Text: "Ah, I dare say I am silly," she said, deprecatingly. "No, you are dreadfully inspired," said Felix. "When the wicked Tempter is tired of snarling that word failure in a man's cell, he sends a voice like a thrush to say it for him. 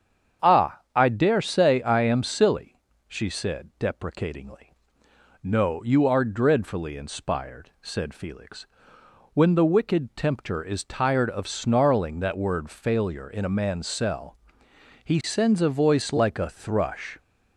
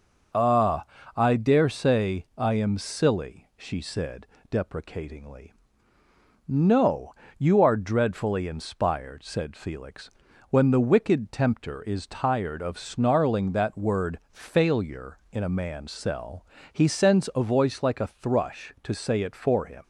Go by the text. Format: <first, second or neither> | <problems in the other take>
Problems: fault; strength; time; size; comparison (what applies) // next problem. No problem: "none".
second | starts louder than the rest; strong; until 1.5 s; 8 dB // stops before "to say it for him"; at 17.1 s